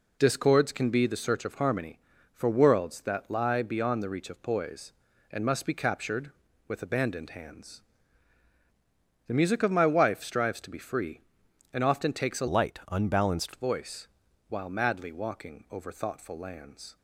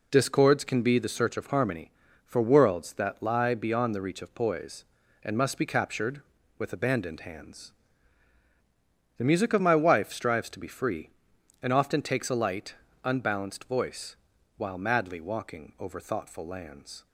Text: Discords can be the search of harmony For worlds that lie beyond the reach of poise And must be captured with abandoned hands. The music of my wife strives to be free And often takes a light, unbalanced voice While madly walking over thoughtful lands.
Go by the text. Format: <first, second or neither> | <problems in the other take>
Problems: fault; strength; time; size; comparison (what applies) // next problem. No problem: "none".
second | changes voice from "light" to "unbalanced"; from 12.4 to 13.5 s; 1.1 s long // pauses between "voice" and "While"; at 14.0 s; 0.40 s long; also in the second